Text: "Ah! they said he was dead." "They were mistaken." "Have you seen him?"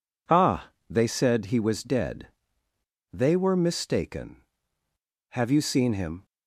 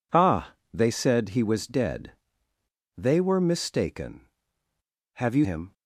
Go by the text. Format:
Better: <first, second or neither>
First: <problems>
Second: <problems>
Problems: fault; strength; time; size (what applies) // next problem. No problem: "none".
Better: first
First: none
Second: skips "seen"; at 5.4 s